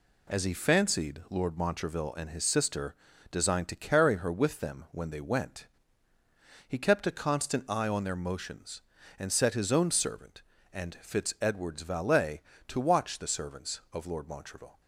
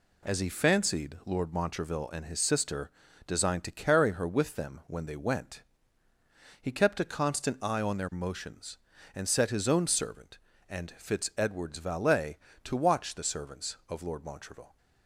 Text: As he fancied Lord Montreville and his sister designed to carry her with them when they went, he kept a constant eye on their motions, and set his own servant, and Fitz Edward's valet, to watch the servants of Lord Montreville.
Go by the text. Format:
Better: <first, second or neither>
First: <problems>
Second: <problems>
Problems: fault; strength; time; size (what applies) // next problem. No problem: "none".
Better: neither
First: pauses between "sister" and "designed"; slight; at 2.9 s; 0.36 s long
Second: pauses between "sister" and "designed"; slight; at 2.8 s; 0.36 s long